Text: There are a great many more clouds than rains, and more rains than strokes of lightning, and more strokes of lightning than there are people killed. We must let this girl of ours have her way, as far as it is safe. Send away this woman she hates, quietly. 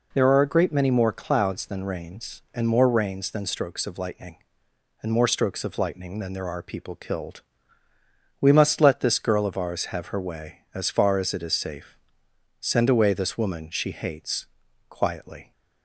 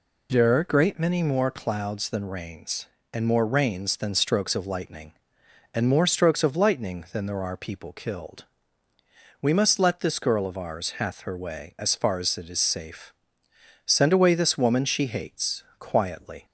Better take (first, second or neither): first